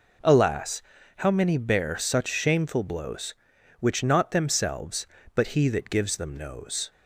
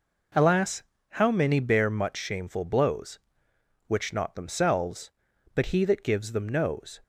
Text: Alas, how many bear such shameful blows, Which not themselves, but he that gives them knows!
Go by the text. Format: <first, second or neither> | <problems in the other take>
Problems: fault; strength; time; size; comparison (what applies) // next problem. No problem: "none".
first | says "much" for "such"; at 1.9 s